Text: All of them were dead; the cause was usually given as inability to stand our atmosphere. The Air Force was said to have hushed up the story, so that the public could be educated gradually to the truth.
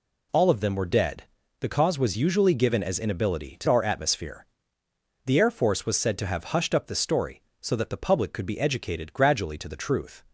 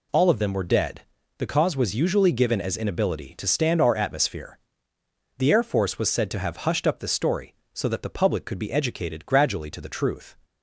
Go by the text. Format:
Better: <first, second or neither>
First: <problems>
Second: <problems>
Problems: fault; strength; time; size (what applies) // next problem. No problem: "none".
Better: second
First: skips "stand"; at 3.6 s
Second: none